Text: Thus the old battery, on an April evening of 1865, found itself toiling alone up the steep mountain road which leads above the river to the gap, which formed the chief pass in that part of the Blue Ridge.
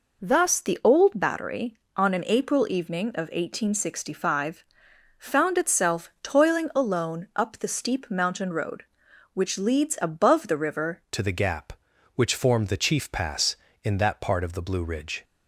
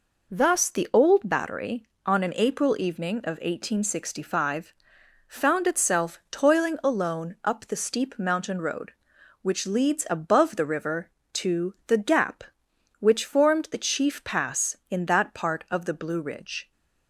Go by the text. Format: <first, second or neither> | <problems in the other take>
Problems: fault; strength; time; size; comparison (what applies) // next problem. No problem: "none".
second | changes voice at "to"; from 11.1 s on; 4.1 s long